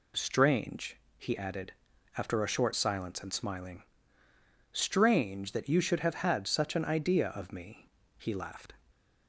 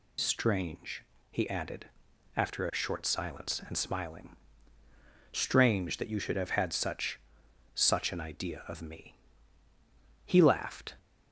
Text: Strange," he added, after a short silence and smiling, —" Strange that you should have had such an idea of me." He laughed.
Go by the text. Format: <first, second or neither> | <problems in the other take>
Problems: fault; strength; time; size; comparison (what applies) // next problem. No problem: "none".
first | says "such" twice; at 7.7 s